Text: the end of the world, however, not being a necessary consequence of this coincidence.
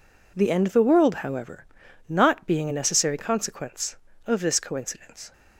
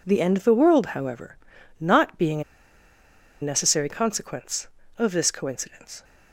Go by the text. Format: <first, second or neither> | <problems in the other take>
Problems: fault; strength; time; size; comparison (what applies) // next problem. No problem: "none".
first | pauses between "a" and "necessary"; at 2.4 s; 1.0 s long